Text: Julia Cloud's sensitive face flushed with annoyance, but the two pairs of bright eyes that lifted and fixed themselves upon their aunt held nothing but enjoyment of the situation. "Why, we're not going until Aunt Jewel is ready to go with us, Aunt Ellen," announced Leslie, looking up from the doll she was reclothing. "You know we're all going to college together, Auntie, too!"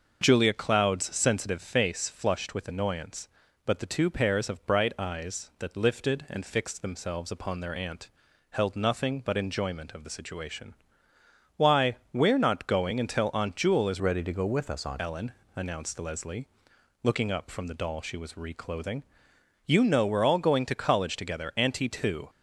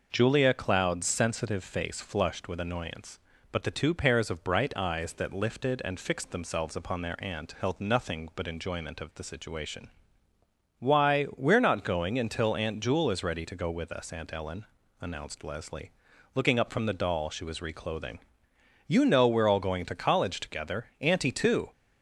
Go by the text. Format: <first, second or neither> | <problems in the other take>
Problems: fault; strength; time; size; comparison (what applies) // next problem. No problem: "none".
second | starts louder than the rest; noticeable; until 1.2 s; 6 dB // pauses between "aunt" and "held"; at 8.0 s; 0.42 s long // changes voice from "ready" to "Aunt"; from 14.0 to 15.0 s; 1.0 s long